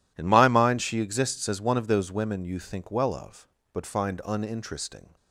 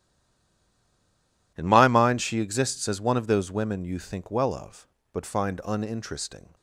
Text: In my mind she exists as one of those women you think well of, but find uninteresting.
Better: first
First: none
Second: stays silent before the first word; noticeable; until 1.5 s; 1.5 s long

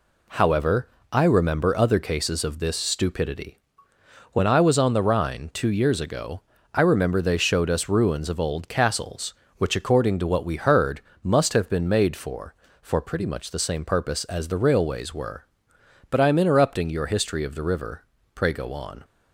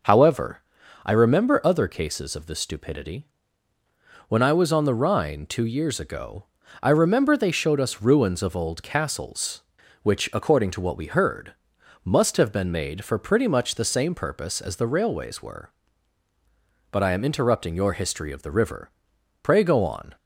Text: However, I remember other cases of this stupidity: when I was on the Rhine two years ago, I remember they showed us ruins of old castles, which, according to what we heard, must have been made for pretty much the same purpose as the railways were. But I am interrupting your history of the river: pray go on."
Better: second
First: says "for" twice; at 12.8 s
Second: none

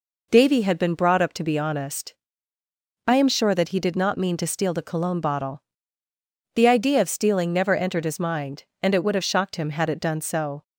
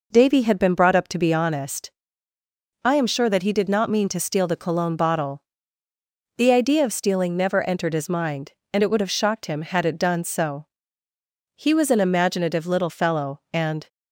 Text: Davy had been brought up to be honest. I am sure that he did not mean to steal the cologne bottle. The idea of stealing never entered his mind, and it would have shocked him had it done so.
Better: first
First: none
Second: goes on to say "He was an imaginative little fellow and"; strong; from 11.5 s on; 2.3 s long

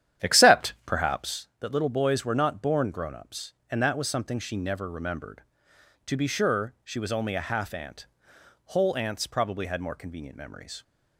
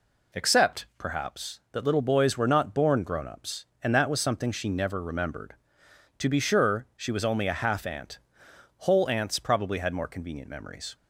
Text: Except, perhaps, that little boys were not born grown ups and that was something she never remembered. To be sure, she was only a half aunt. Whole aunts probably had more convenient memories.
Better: second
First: starts louder than the rest; strong; until 1.5 s; 10.5 dB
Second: none

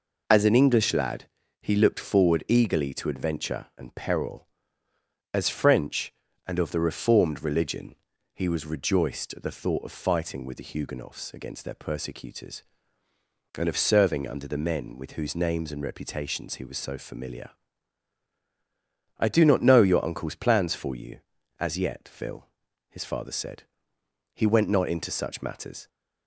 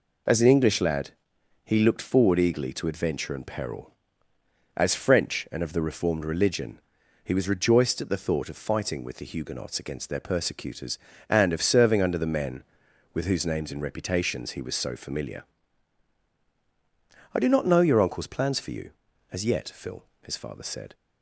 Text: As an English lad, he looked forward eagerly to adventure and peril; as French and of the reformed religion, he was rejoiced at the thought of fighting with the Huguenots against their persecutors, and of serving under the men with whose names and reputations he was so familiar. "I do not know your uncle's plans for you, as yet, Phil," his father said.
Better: second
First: goes on to say "He went not into such matters"; from 24.3 s on; 1.5 s long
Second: none

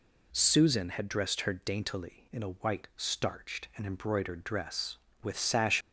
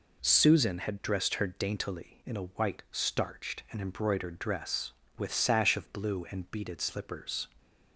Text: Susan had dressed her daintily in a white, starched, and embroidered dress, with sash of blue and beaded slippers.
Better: second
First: stops before "of blue and beaded slippers"; at 5.8 s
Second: none

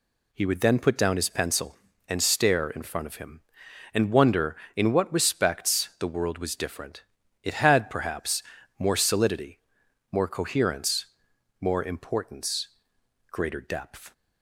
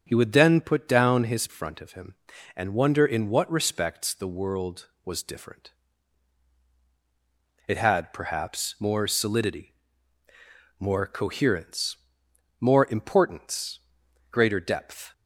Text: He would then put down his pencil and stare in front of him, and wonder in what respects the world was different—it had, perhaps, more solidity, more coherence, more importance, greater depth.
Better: first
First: none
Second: starts louder than the rest; strong; until 1.0 s; 7 dB // skips "pencil and stare in"; at 1.4 s

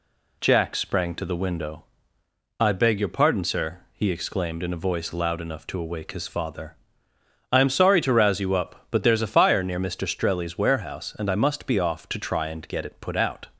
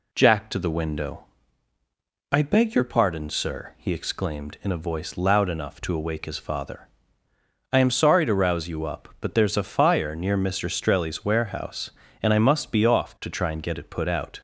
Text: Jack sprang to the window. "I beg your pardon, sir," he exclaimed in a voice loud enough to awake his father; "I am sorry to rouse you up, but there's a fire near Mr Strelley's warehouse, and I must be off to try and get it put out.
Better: first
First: none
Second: skips "sprang"; at 0.4 s

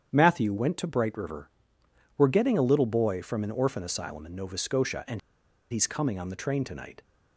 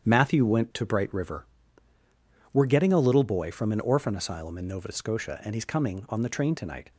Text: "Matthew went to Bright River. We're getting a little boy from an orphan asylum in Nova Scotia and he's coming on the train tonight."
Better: second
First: starts louder than the rest; strong; until 1.1 s; 8.5 dB // pauses between "and" and "he's"; noticeable; at 5.1 s; 0.50 s long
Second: starts louder than the rest; strong; until 1.1 s; 8.5 dB

